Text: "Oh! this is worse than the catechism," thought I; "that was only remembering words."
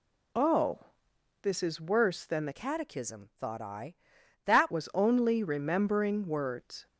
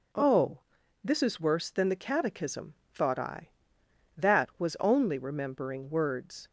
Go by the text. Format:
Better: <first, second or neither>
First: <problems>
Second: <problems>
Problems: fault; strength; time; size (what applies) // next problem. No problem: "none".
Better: second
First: changes voice from "catechism" to "that"; from 2.5 to 4.7 s; 2.2 s long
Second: none